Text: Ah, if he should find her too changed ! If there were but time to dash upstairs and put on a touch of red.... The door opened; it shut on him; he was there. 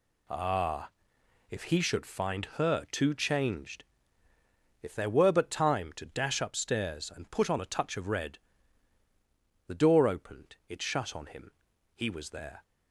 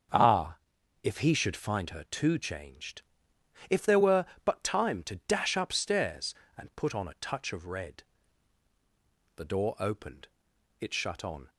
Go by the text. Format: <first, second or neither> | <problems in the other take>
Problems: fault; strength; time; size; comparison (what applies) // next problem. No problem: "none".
first | starts louder than the rest; strong; until 1.6 s; 7.5 dB // stops before "him he was there"; at 11.4 s